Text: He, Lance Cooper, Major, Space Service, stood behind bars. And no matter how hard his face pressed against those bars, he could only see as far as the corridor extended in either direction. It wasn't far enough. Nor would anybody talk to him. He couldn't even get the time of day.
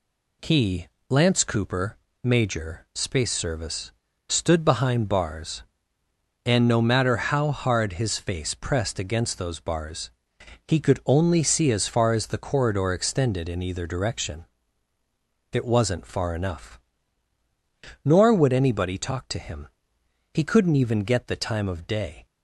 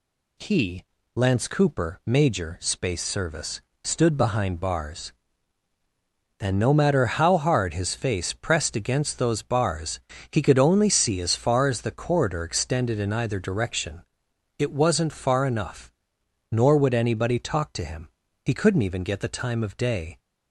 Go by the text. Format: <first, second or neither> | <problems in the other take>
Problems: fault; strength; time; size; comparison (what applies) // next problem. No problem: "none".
neither | none